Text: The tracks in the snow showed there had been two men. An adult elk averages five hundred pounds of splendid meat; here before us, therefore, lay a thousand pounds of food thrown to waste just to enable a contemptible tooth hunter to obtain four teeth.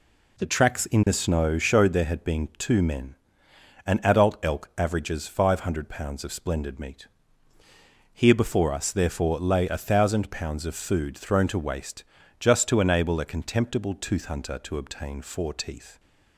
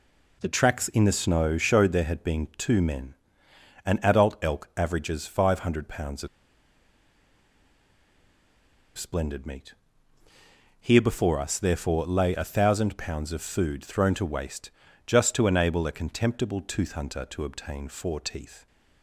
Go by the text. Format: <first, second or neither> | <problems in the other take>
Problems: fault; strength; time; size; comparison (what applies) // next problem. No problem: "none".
first | pauses between "of" and "splendid"; strong; at 6.2 s; 2.7 s long // pauses between "waste" and "just"; slight; at 14.7 s; 0.36 s long; slight in the first